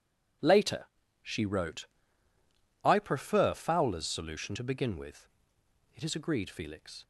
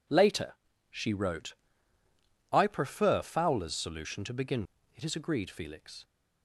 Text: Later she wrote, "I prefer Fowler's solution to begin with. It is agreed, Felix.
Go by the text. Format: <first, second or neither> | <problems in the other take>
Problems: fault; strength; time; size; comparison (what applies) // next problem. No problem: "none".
first | pauses between "Later" and "she"; at 0.5 s; 0.38 s long; also in the first // skips "with"; at 4.7 s